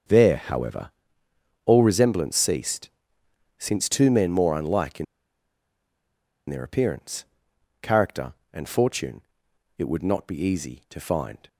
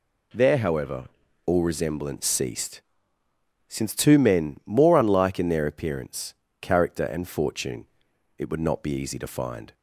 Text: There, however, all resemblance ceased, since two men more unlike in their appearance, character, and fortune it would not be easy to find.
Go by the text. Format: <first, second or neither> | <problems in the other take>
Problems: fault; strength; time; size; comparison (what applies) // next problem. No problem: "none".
second | starts louder than the rest; until 1.8 s; 7 dB // pauses between "in" and "their"; strong; at 5.0 s; 1.4 s long // pauses between "fortune" and "it"; noticeable; at 9.2 s; 0.56 s long; noticeable in the second